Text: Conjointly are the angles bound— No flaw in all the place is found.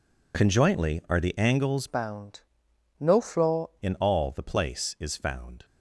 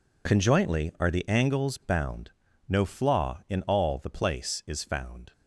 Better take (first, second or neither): second